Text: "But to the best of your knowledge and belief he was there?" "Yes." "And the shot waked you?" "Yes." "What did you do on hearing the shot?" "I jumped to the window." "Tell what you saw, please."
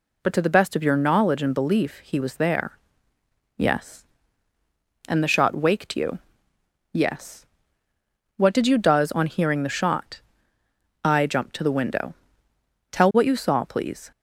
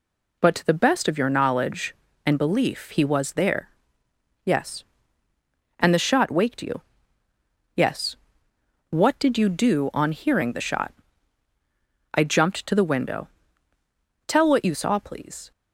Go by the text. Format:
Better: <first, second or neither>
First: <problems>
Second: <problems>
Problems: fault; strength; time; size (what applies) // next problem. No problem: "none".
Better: second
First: says "does" for "do"; at 8.7 s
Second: none